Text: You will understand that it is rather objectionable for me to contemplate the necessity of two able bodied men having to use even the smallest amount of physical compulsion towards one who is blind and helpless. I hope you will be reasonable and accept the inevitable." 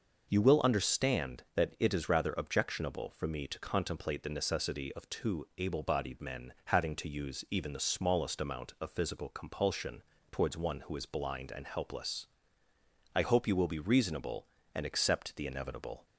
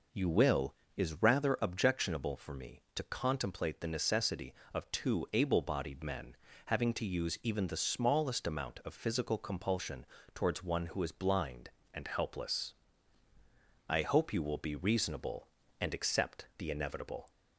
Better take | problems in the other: first | skips "understand that it"; at 0.8 s // pauses between "men" and "having"; slight; at 6.3 s; 0.30 s long // pauses between "compulsion" and "towards"; slight; at 10.0 s; 0.30 s long; slight in the first

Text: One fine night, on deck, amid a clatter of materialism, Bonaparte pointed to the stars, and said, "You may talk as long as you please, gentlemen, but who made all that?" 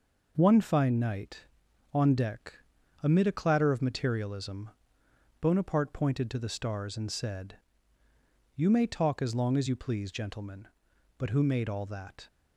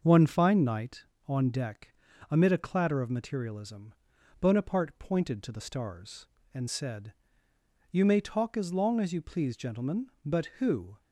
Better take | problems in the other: first | starts louder than the rest; noticeable; until 1.0 s; 6 dB // stops before "made all that"; at 10.9 s

